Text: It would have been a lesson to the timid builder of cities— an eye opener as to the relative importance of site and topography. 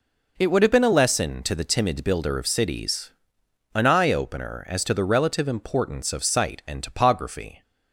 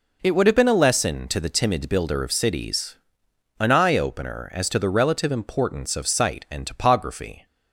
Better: neither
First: none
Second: none

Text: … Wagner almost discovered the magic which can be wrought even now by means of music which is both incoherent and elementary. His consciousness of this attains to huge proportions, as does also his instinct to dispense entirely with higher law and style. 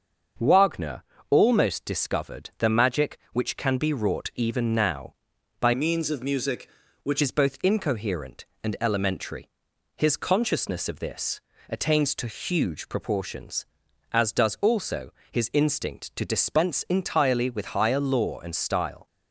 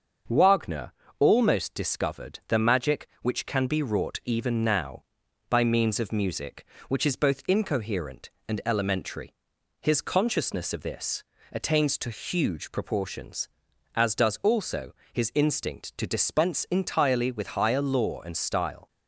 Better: second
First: starts louder than the rest; until 1.6 s; 6.5 dB // pauses between "Wagner" and "almost"; slight; at 1.0 s; 0.30 s long // changes voice from "means" to "which"; from 5.7 to 7.2 s; 1.5 s long // pauses between "this" and "attains"; slight; at 11.3 s; 0.30 s long // pauses between "also" and "his"; slight; at 15.1 s; 0.18 s long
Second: starts louder than the rest; until 1.5 s; 6.5 dB // pauses between "Wagner" and "almost"; slight; at 0.9 s; 0.30 s long // pauses between "this" and "attains"; slight; at 11.2 s; 0.30 s long // pauses between "also" and "his"; slight; at 14.9 s; 0.18 s long

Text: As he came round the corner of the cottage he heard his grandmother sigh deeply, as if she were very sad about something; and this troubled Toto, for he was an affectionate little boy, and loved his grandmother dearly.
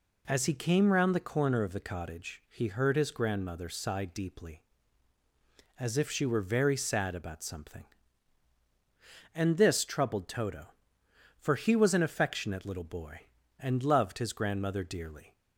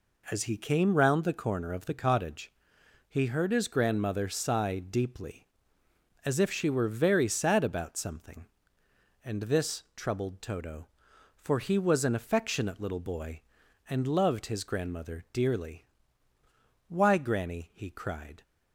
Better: first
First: none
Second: pauses between "cottage" and "he"; noticeable; at 2.5 s; 0.58 s long // goes on to say "Why Granny he cried"; from 16.8 s on; 1.5 s long

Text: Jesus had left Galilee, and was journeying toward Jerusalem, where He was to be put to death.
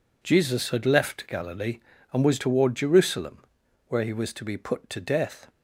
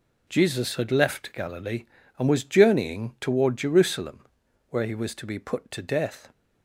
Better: second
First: skips "journeying"; at 2.3 s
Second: none

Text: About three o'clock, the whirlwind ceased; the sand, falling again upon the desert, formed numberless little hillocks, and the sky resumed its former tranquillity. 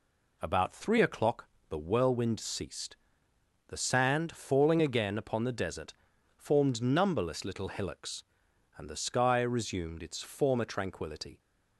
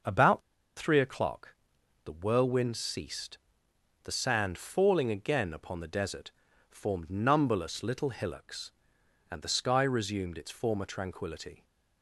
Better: first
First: none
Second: pauses between "About" and "three"; at 0.3 s; 0.36 s long

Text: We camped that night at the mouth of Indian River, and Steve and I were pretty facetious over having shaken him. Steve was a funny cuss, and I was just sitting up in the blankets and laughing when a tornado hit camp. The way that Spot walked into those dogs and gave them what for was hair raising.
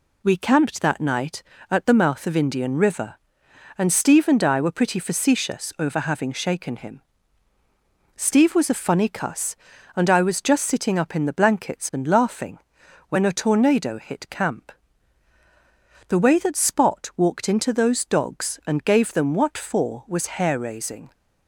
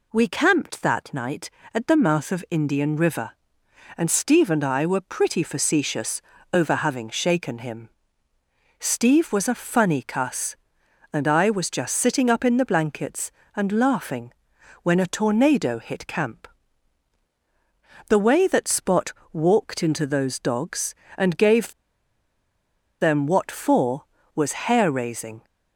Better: first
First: pauses between "laughing" and "when"; noticeable; at 12.5 s; 0.50 s long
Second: pauses between "facetious" and "over"; slight; at 6.2 s; 0.32 s long // pauses between "laughing" and "when"; noticeable; at 14.3 s; 0.52 s long // pauses between "Spot" and "walked"; slight; at 19.1 s; 0.20 s long // pauses between "gave" and "them"; strong; at 21.7 s; 1.2 s long

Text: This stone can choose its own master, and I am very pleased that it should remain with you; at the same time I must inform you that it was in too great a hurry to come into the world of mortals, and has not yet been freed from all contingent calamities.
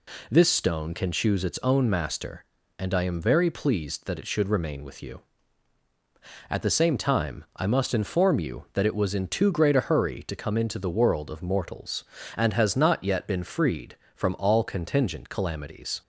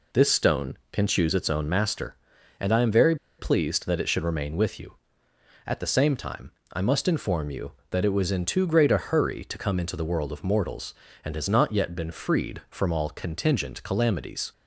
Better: first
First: none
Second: pauses between "very" and "pleased"; slight; at 3.1 s; 0.23 s long // pauses between "time" and "I"; slight; at 6.5 s; 0.20 s long

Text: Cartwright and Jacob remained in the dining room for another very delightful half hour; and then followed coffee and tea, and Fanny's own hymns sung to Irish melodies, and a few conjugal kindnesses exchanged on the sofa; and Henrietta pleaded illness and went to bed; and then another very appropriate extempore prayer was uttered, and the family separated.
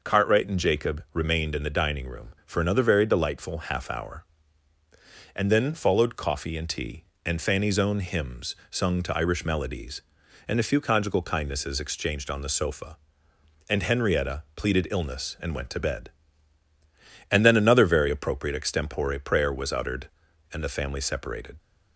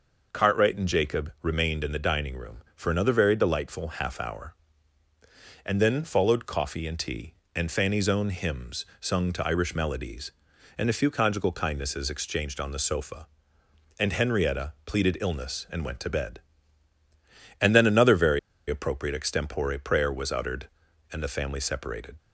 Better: first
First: pauses between "hymns" and "sung"; slight; at 8.5 s; 0.16 s long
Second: pauses between "hymns" and "sung"; slight; at 8.8 s; 0.16 s long // pauses between "very" and "appropriate"; slight; at 18.3 s; 0.29 s long

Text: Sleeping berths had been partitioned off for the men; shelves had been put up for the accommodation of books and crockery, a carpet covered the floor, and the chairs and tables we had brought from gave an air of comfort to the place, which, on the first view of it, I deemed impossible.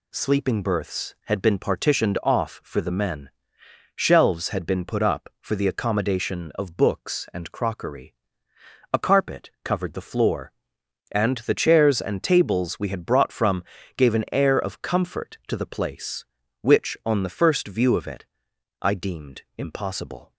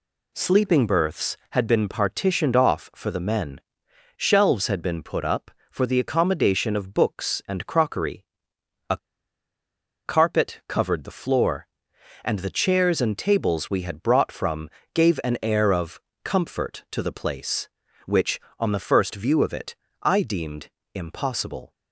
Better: first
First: pauses between "from" and "gave"; slight; at 13.6 s; 0.34 s long // pauses between "deemed" and "impossible"; slight; at 19.4 s; 0.16 s long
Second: pauses between "a" and "carpet"; at 8.9 s; 1.0 s long // pauses between "from" and "gave"; slight; at 14.6 s; 0.24 s long // pauses between "of" and "comfort"; slight; at 16.0 s; 0.24 s long // pauses between "deemed" and "impossible"; slight; at 20.6 s; 0.26 s long

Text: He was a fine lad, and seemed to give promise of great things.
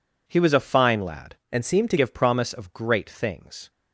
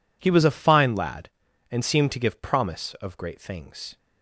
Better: second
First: changes voice from "and" to "to"; from 1.4 to 1.9 s; 0.5 s long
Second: none

